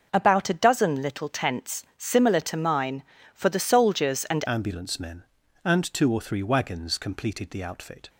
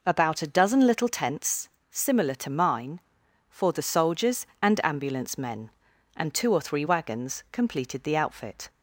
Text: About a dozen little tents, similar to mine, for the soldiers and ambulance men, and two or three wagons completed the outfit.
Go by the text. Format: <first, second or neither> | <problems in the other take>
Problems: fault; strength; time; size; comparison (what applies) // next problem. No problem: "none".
second | starts louder than the rest; until 1.1 s; 6 dB // changes voice at "ambulance"; from 4.4 s on; 3.6 s long